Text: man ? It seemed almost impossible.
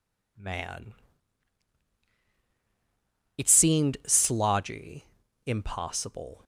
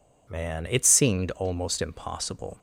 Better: second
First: says "slodgy" for "almost"; at 4.0 s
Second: none

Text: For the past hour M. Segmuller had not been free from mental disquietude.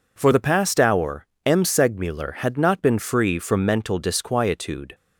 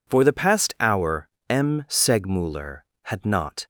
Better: first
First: pauses between "hour" and "M"; slight; at 1.2 s; 0.18 s long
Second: pauses between "hour" and "M"; slight; at 1.2 s; 0.22 s long // stops before "been free from mental disquietude"; at 3.6 s

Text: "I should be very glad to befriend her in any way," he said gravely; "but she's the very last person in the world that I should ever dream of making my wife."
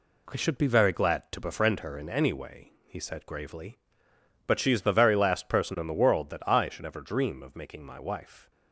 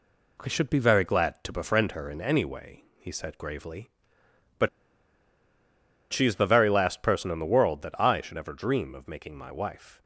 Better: first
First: none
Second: pauses between "but" and "she's"; strong; at 4.6 s; 1.4 s long

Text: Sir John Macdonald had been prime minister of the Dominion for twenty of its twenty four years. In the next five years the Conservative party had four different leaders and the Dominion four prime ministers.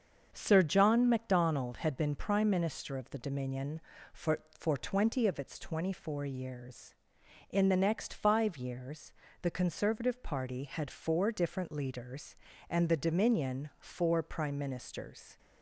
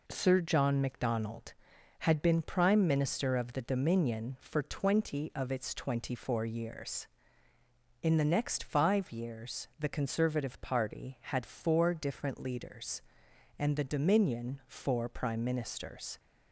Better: second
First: starts louder than the rest; until 1.3 s; 7 dB // says "for" twice; at 4.5 s // pauses between "years" and "the"; slight; at 9.1 s; 0.30 s long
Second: none

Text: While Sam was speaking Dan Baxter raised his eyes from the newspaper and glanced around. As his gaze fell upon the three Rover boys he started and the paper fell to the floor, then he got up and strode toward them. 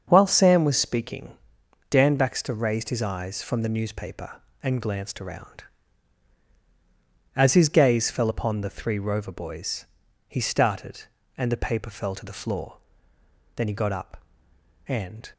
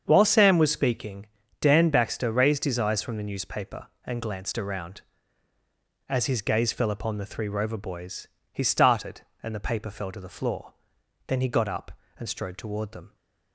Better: second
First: starts louder than the rest; until 1.0 s; 7 dB // pauses between "speaking" and "Dan"; noticeable; at 1.3 s; 0.58 s long // pauses between "boys" and "he"; at 9.8 s; 0.44 s long // stops before "strode toward them"; at 15.3 s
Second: starts louder than the rest; strong; until 1.0 s; 7 dB // pauses between "speaking" and "Dan"; slight; at 1.2 s; 0.32 s long // pauses between "boys" and "he"; slight; at 8.2 s; 0.26 s long

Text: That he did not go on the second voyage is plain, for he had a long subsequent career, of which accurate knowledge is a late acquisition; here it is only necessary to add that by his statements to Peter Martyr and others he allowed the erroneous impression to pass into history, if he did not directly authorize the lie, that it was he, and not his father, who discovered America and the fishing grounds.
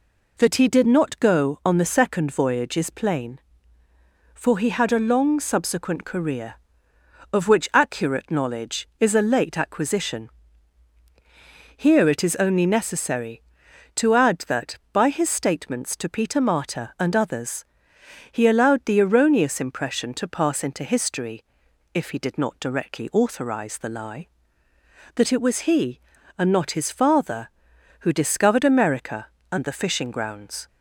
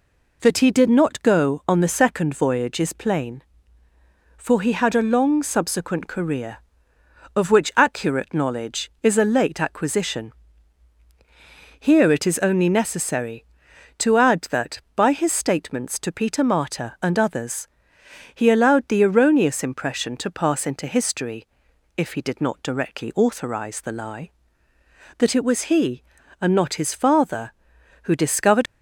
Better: first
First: pauses between "others" and "he"; noticeable; at 17.6 s; 0.66 s long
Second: pauses between "others" and "he"; noticeable; at 17.6 s; 0.66 s long // stops before "America and the fishing grounds"; at 28.6 s

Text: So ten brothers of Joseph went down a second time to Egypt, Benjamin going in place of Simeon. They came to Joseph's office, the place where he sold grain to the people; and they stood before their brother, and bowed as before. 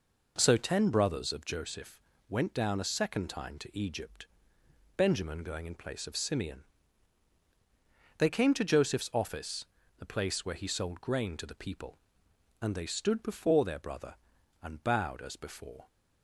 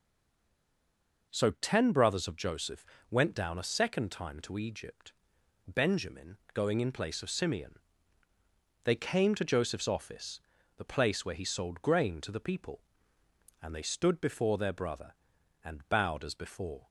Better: first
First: pauses between "Joseph" and "went"; slight; at 1.9 s; 0.30 s long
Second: stays silent before the first word; noticeable; until 1.3 s; 1.3 s long // pauses between "Joseph" and "went"; slight; at 2.8 s; 0.24 s long // pauses between "Benjamin" and "going"; slight; at 6.3 s; 0.16 s long

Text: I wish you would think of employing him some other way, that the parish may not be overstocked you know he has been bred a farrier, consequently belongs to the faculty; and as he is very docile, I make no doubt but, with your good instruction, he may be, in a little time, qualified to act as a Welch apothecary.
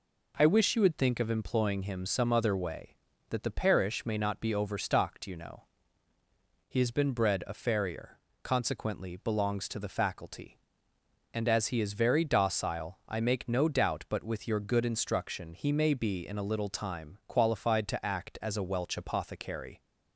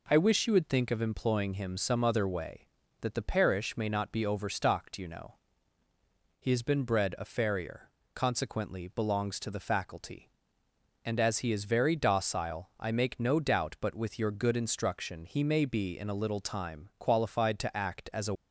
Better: first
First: pauses between "know" and "he"; at 5.6 s; 1.0 s long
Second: pauses between "know" and "he"; at 5.3 s; 1.0 s long // stops before "Welch apothecary"; at 18.3 s

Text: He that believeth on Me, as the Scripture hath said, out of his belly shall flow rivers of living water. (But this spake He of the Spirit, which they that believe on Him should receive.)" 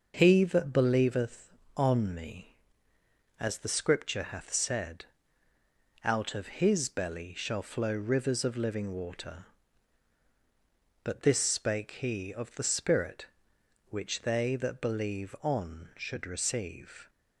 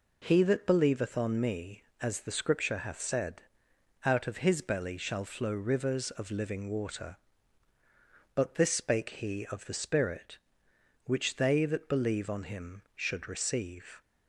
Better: second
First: skips "Him"; at 15.9 s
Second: none

